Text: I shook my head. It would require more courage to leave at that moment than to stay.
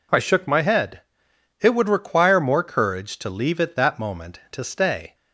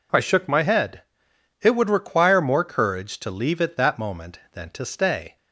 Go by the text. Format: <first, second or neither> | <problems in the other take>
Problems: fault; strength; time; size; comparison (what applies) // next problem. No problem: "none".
second | skips "than"; at 4.4 s